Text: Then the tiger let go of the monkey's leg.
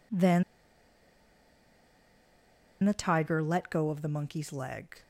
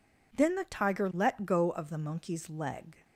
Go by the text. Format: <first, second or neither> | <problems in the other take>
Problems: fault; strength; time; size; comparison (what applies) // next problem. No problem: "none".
second | pauses between "Then" and "the"; strong; at 0.4 s; 2.4 s long